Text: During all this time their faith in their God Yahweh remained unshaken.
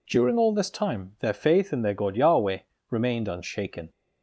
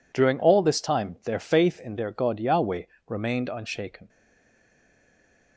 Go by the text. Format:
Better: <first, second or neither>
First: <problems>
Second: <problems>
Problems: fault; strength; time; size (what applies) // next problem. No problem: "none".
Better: first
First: pauses between "Yahweh" and "remained"; slight; at 2.6 s; 0.28 s long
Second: pauses between "Yahweh" and "remained"; slight; at 2.8 s; 0.22 s long // stays silent after the last word; noticeable; from 4.0 s on; 1.5 s long